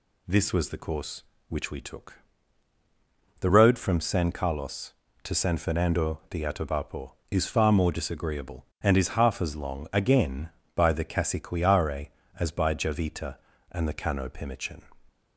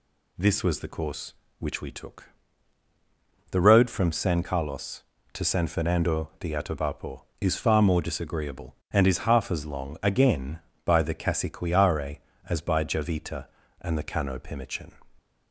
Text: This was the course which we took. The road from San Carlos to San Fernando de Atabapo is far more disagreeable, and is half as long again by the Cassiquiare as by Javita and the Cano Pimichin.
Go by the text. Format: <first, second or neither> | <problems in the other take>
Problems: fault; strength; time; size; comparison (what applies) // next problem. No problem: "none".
neither | none